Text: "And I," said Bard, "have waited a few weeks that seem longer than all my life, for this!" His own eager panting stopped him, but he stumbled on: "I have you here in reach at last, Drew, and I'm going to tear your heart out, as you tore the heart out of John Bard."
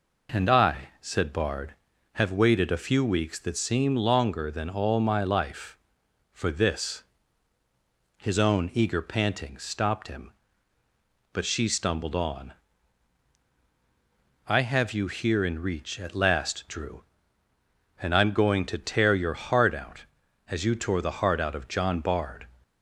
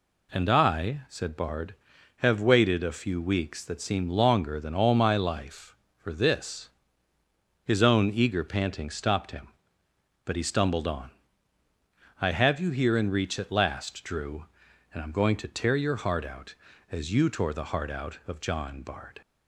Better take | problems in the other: second | says "she" for "he"; at 11.4 s

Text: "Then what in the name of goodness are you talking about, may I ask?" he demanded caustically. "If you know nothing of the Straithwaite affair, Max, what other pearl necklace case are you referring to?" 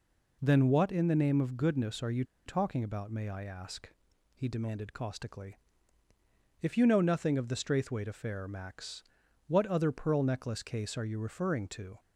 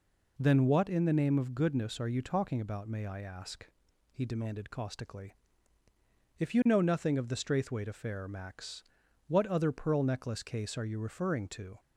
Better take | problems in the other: second | pauses between "you" and "talking"; slight; at 2.2 s; 0.23 s long

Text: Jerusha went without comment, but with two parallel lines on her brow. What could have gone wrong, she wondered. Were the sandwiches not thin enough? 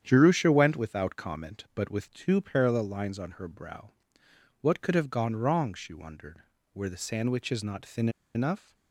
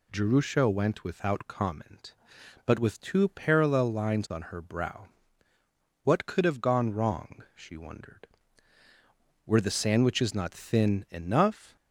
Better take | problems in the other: second | starts louder than the rest; strong; until 1.0 s; 9 dB // pauses between "thin" and "enough"; slight; at 8.0 s; 0.26 s long

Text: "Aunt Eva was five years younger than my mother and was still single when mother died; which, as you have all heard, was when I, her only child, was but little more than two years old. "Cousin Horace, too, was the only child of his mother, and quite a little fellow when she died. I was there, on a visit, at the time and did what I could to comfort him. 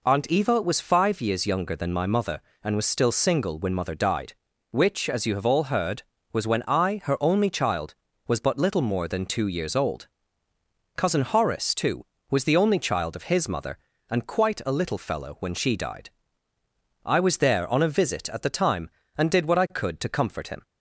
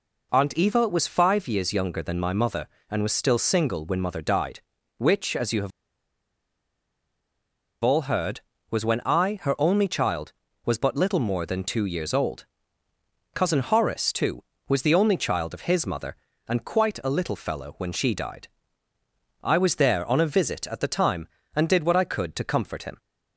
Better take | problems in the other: first | pauses between "have" and "all"; strong; at 5.7 s; 2.1 s long

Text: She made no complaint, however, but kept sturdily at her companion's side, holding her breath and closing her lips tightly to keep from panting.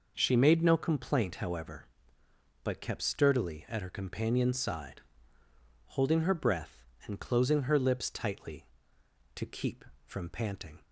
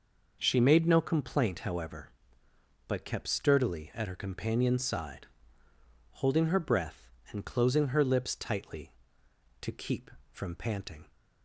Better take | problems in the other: neither | none

